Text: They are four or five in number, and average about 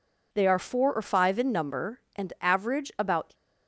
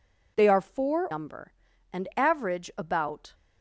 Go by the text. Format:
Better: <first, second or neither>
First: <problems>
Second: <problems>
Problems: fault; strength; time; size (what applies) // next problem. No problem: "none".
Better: first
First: none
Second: skips "or five in"; at 1.0 s